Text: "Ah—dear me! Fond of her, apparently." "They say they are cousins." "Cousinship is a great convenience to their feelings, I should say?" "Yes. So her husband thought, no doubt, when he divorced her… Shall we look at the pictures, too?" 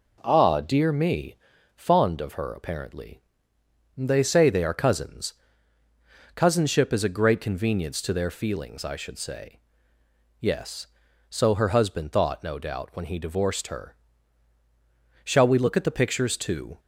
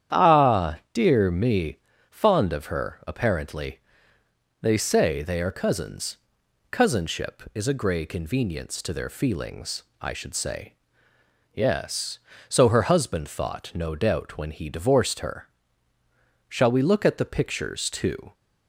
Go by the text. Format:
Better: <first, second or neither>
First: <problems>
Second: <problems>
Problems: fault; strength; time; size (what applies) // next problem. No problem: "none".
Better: first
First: none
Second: starts louder than the rest; strong; until 1.2 s; 9.5 dB // says "grey" for "great"; at 7.7 s